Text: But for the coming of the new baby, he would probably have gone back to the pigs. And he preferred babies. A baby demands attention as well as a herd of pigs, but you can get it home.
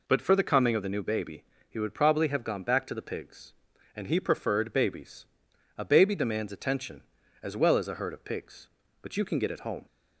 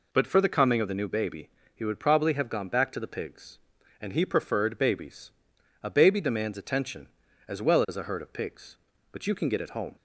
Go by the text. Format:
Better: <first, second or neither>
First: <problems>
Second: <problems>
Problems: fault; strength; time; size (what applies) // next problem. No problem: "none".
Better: neither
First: none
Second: none